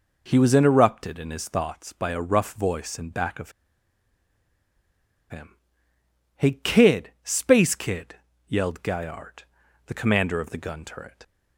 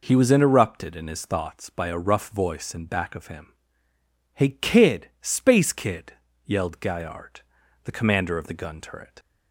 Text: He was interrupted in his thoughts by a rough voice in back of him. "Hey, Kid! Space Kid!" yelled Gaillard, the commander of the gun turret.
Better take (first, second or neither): second